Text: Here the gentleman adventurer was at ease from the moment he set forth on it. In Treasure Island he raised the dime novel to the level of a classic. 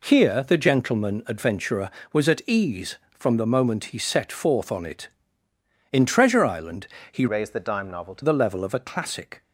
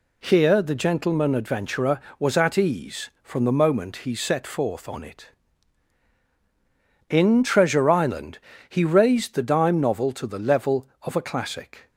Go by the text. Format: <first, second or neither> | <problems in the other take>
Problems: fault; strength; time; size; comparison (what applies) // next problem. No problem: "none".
second | pauses between "Island" and "he"; slight; at 6.8 s; 0.24 s long; slight in the second // changes voice from "raised" to "to"; from 7.2 to 8.2 s; 1.0 s long